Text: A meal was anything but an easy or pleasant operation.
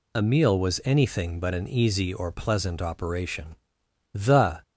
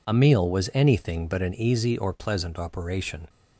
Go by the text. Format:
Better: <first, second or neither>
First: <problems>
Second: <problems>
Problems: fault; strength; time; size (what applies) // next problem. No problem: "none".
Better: second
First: goes on to say "The"; from 4.1 s on; 0.50 s long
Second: none